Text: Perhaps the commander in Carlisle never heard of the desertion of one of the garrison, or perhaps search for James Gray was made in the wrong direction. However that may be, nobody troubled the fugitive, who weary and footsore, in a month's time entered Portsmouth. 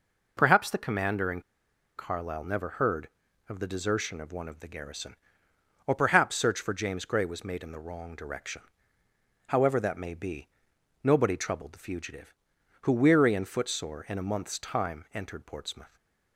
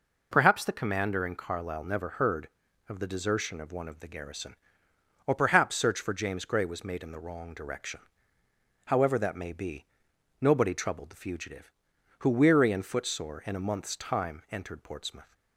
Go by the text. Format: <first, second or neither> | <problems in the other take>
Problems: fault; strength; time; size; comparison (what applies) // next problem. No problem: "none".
second | pauses between "in" and "Carlisle"; noticeable; at 1.4 s; 0.57 s long